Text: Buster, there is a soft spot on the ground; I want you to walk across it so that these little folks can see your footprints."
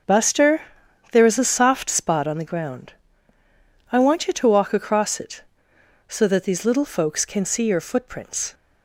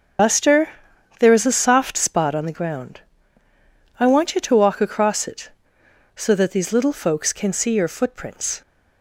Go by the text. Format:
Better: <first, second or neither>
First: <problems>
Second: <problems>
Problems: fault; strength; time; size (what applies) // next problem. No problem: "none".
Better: first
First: starts louder than the rest; until 1.5 s; 6.5 dB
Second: loses the start of "Buster"; at 0.1 s; 60 ms // starts louder than the rest; strong; until 1.7 s; 7.5 dB